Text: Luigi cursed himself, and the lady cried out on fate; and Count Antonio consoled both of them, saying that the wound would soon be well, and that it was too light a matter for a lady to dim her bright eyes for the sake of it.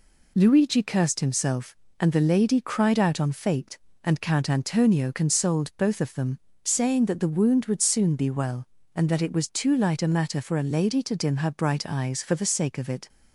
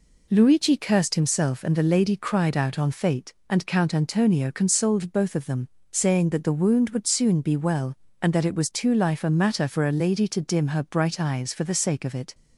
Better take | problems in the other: first | says "life" for "light"; at 8.9 s

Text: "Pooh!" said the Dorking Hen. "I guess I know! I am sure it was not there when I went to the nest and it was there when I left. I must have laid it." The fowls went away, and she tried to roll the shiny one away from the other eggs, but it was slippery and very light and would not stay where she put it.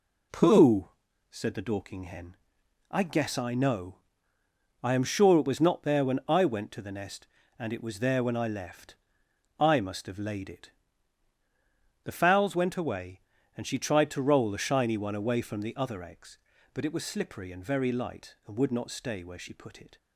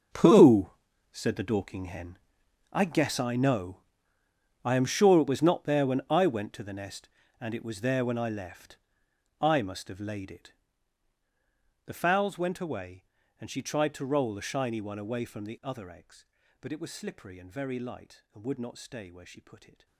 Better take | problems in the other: first | gets quieter; strong; throughout; 15.5 dB

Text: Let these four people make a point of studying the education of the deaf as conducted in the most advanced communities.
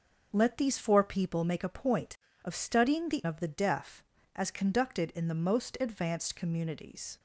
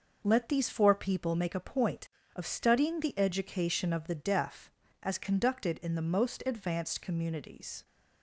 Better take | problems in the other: second | skips "education"; at 3.2 s

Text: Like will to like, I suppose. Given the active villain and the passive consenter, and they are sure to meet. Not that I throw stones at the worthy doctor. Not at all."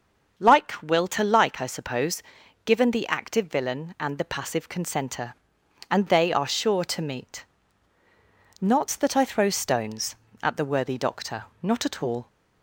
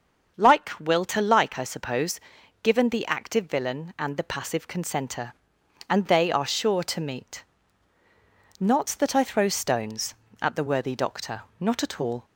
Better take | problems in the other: neither | starts louder than the rest; the same in both

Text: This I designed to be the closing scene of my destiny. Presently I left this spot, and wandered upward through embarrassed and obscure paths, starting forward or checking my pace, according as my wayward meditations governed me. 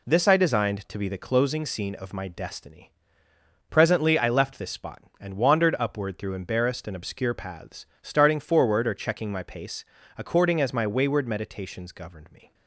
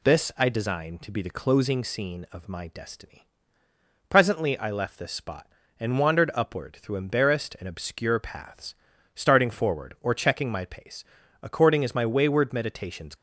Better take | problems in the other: first | stops before "governed me"; at 13.1 s

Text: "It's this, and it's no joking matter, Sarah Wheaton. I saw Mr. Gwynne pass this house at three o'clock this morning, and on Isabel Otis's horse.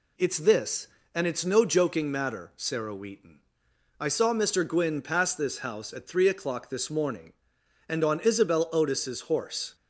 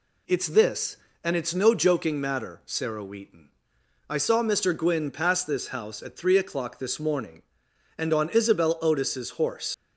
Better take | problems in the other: first | leaves "horse" unfinished; at 9.7 s; 100 ms

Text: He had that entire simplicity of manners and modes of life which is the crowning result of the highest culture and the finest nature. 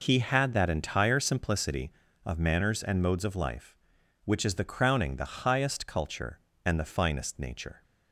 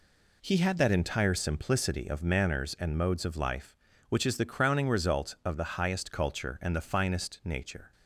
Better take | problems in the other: second | skips "result of"; at 5.1 s

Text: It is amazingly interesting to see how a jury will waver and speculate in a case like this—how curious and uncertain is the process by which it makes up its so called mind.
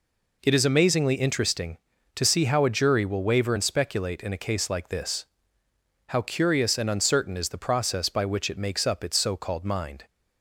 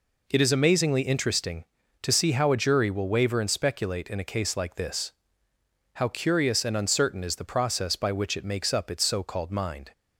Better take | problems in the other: neither | none

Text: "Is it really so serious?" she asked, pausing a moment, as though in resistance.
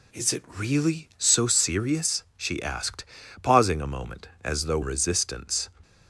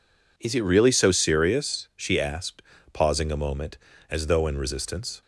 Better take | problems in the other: second | skips "in"; at 4.8 s

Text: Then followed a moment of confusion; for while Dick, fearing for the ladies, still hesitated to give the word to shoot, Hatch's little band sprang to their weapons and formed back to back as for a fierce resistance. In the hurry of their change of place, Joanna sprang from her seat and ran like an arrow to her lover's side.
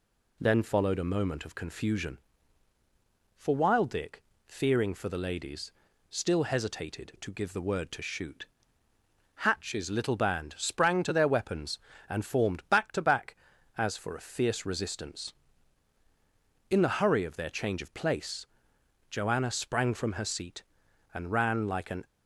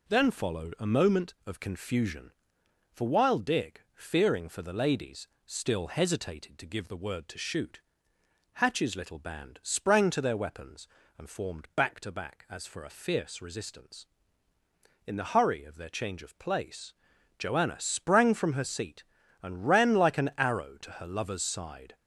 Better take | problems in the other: second | stops before "arrow to her lover's side"; at 22.0 s

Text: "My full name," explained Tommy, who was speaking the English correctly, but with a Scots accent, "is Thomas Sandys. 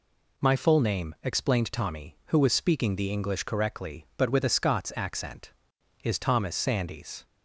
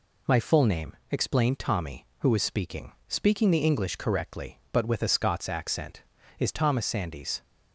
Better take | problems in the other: first | says "speaking" twice; at 3.0 s

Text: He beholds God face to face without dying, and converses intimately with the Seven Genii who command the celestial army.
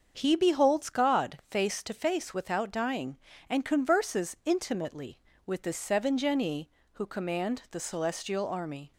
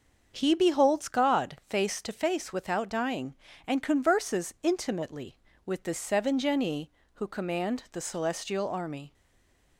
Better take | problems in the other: first | starts louder than the rest; until 1.3 s; 6.5 dB; also in the first // stays silent after the last word; slight; from 9.1 s on; 0.6 s long

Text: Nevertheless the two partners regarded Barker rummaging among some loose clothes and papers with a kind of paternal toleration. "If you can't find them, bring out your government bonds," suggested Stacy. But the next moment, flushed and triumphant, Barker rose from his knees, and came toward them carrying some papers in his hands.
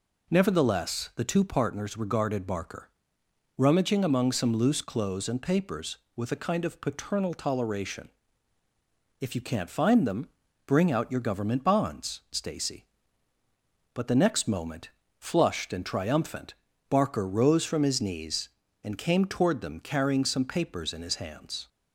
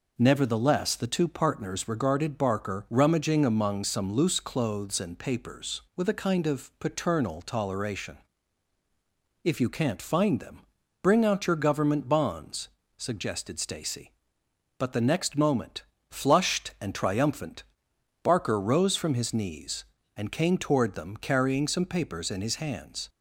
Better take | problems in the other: second | pauses between "Barker" and "rummaging"; noticeable; at 2.8 s; 0.70 s long // skips "suggested"; at 12.2 s

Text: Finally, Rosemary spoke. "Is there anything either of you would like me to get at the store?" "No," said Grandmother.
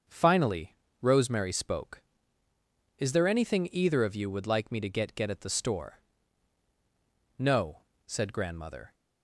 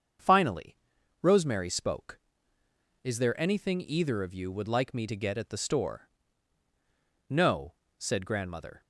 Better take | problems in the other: second | starts louder than the rest; until 1.3 s; 6.5 dB; also in the second // says "get" twice; at 5.1 s

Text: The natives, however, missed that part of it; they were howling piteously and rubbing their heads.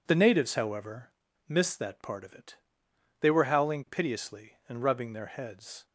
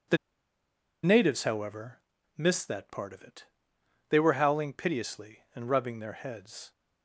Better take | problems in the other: first | pauses between "The" and "natives"; noticeable; at 0.1 s; 0.86 s long

